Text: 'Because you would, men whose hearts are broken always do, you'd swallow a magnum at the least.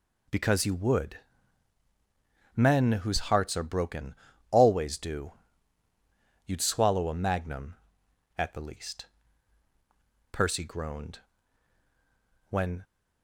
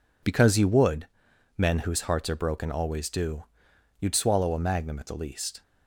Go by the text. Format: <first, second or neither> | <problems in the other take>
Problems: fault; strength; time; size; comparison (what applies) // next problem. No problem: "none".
second | pauses between "broken" and "always"; slight; at 4.1 s; 0.36 s long // goes on to say "Percy groaned When"; strong; from 10.3 s on; 2.5 s long